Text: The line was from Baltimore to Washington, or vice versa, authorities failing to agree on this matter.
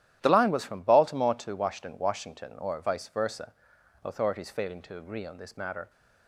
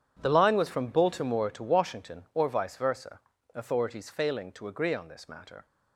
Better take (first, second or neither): second